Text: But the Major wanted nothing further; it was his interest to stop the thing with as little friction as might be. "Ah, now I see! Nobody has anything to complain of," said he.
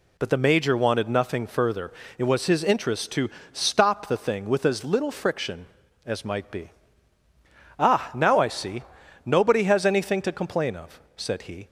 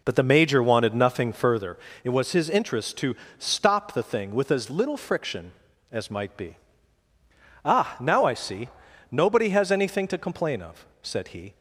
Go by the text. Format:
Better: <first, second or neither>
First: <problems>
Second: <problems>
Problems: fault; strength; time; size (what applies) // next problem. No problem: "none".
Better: first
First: pauses between "to" and "stop"; slight; at 3.2 s; 0.24 s long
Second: starts louder than the rest; noticeable; until 1.7 s; 4.5 dB // pauses between "to" and "stop"; slight; at 3.1 s; 0.24 s long